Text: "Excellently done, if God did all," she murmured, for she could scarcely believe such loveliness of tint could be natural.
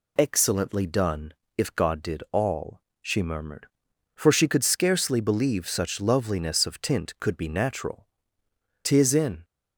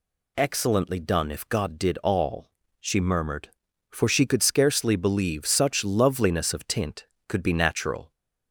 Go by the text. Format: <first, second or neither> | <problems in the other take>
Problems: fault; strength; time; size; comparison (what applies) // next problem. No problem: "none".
second | goes on to say "Tis in"; from 8.8 s on; 0.60 s long